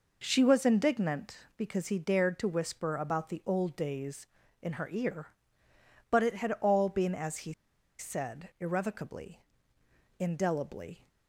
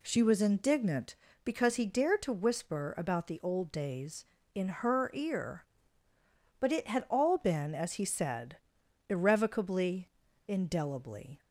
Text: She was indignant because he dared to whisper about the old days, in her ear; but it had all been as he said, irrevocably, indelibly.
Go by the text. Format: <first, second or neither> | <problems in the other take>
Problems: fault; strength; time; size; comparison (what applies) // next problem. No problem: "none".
second | pauses between "he" and "said"; noticeable; at 7.5 s; 0.46 s long